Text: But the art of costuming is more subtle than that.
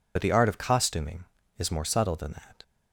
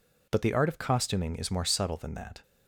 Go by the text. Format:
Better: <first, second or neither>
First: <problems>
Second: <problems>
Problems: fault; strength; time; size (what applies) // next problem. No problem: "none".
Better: second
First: loses the start of "But"; at 0.1 s; 50 ms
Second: none